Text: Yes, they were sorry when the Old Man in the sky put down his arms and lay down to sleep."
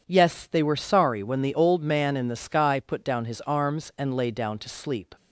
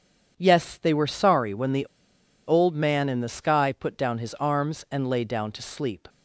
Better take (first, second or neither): first